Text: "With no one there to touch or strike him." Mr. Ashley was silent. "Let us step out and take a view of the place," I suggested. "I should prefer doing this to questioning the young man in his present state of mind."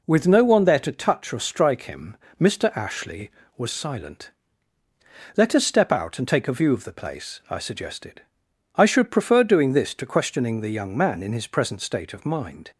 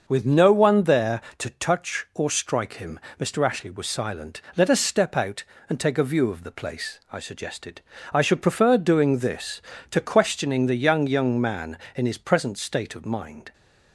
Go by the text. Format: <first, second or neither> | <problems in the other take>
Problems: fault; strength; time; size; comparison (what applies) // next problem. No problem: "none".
first | starts louder than the rest; noticeable; until 1.0 s; 6 dB // says "young" twice; at 11.0 s